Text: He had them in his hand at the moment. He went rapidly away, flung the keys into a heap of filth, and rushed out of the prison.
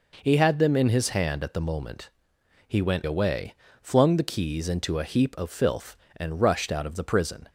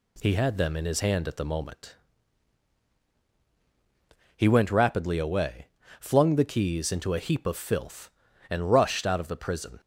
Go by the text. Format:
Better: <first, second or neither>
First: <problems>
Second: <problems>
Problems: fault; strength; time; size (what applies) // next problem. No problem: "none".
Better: second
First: skips "rapidly"; at 3.0 s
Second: none